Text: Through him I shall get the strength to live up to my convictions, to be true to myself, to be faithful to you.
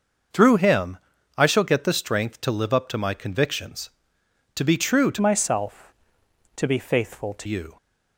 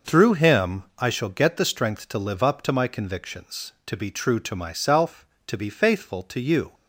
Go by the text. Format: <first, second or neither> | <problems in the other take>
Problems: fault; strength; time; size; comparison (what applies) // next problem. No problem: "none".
second | starts louder than the rest; until 1.7 s; 6.5 dB // pauses between "him" and "I"; at 0.9 s; 0.40 s long; slight in the second // changes voice from "myself" to "to"; from 5.2 to 7.4 s; 2.2 s long